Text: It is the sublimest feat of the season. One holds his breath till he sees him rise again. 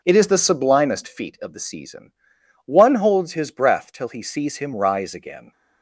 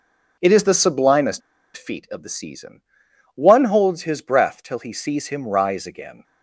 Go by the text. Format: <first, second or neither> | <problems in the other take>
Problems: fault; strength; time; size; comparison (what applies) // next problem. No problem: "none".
first | pauses between "sublimest" and "feat"; at 1.4 s; 0.36 s long